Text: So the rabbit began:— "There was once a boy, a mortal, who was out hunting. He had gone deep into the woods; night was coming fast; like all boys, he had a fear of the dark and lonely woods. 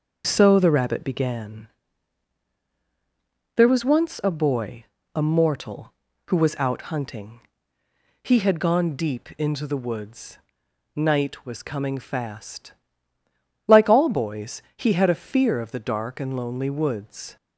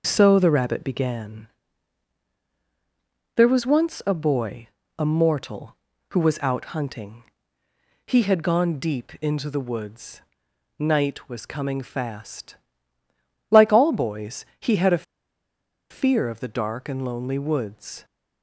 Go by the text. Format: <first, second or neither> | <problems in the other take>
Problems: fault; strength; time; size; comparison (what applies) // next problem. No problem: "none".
first | starts louder than the rest; noticeable; until 1.0 s; 6 dB; also in the first // pauses between "a" and "fear"; noticeable; at 15.0 s; 0.86 s long